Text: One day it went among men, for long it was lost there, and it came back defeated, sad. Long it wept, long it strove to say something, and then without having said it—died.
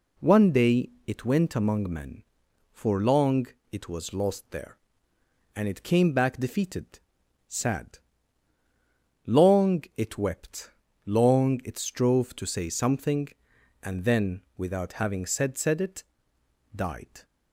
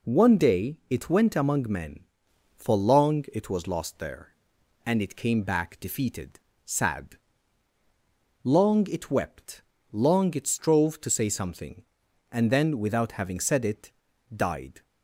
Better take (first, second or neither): second